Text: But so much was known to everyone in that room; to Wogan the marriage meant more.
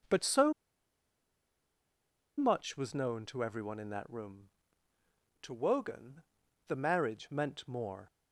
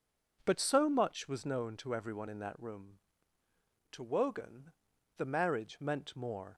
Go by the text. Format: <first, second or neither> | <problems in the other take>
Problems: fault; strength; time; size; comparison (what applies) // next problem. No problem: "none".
second | pauses between "so" and "much"; strong; at 0.5 s; 1.8 s long // pauses between "Wogan" and "the"; noticeable; at 6.2 s; 0.46 s long; noticeable in the second